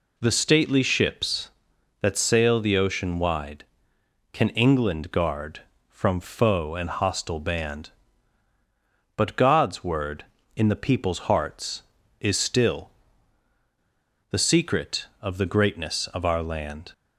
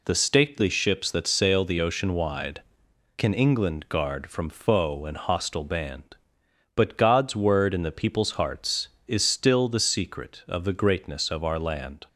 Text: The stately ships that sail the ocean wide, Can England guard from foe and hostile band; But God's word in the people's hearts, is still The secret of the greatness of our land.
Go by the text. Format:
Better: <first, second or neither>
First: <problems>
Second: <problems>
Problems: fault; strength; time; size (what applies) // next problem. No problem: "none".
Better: second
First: pauses between "still" and "The"; strong; at 12.8 s; 1.4 s long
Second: none